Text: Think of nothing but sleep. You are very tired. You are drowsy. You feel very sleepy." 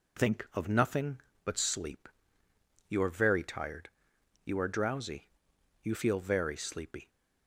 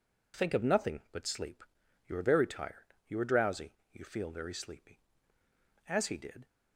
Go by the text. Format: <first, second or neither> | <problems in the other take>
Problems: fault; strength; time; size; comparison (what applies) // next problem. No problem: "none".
first | goes on to say "As he did"; from 5.8 s on; 0.58 s long